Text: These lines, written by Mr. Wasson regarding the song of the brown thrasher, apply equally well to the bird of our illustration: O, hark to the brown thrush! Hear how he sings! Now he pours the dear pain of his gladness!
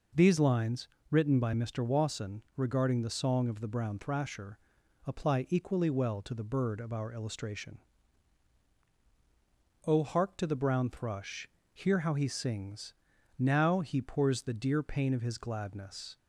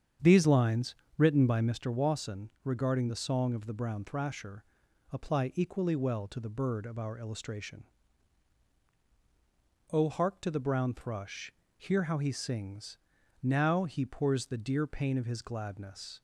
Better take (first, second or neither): first